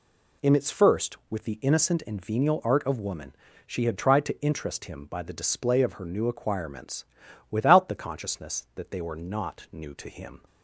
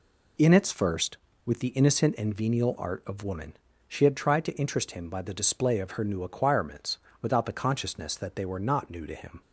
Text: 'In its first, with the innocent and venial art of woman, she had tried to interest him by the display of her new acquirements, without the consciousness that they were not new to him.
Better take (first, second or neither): neither